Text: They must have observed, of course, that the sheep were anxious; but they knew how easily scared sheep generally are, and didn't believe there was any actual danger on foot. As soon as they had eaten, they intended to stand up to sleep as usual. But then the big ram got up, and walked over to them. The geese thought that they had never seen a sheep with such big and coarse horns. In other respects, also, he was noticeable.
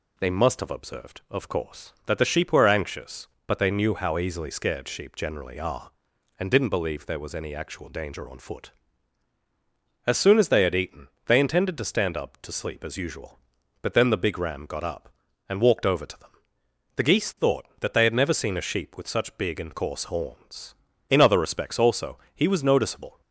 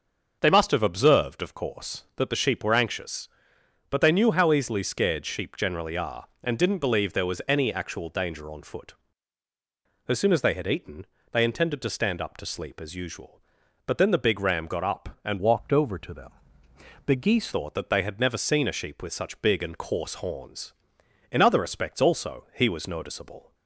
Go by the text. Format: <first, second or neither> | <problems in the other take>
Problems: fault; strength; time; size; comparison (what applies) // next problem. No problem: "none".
first | starts louder than the rest; until 1.4 s; 6.5 dB // changes voice from "walked" to "geese"; from 15.3 to 17.5 s; 2.2 s long